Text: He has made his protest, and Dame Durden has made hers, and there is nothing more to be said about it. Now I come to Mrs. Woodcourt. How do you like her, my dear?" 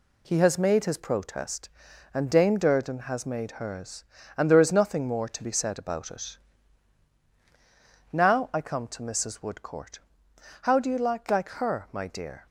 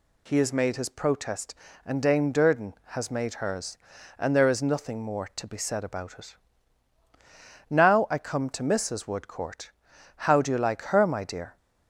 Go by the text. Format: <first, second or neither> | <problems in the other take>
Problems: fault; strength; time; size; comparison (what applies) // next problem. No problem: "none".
second | says "like" twice; at 11.2 s